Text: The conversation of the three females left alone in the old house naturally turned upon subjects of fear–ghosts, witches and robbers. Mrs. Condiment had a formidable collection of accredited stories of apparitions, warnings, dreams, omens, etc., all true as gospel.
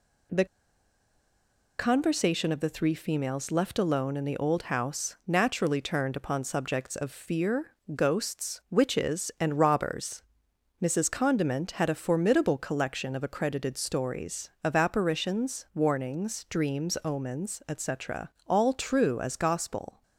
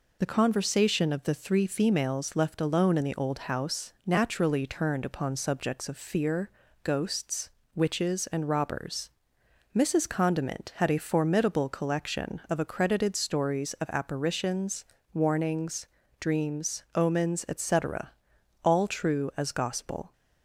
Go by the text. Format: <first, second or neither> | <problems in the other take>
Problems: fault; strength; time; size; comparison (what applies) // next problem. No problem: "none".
second | pauses between "The" and "conversation"; strong; at 0.4 s; 1.3 s long